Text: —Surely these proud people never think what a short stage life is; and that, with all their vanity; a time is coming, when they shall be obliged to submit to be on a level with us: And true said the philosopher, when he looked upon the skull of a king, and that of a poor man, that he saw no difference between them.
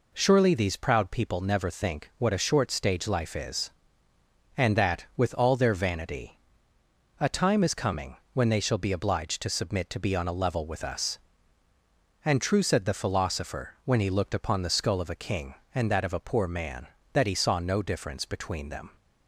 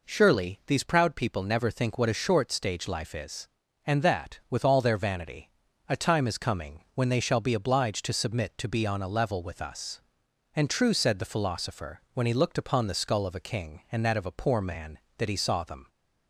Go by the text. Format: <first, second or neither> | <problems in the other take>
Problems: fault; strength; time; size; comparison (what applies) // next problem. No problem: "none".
first | skips "no difference between"; at 15.6 s